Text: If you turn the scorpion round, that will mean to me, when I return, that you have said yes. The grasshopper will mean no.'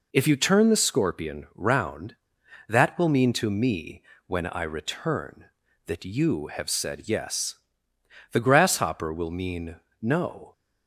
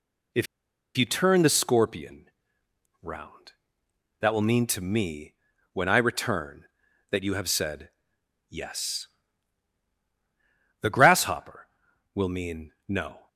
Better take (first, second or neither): first